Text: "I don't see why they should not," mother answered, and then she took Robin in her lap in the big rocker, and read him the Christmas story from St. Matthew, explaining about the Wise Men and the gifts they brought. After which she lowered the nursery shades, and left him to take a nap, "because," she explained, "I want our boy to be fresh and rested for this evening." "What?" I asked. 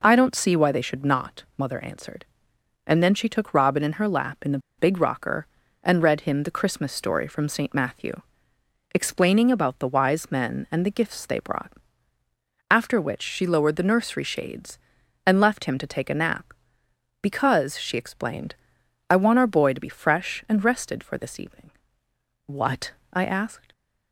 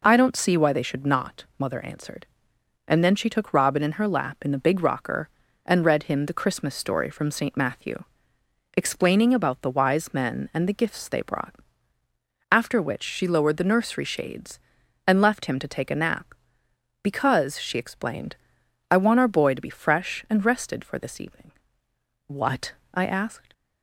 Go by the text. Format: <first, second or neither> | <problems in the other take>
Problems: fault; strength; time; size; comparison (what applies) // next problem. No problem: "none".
second | pauses between "the" and "big"; slight; at 4.5 s; 0.19 s long